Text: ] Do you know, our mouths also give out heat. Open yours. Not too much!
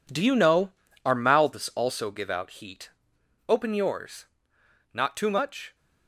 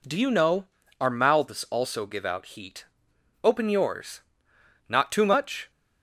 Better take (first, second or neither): second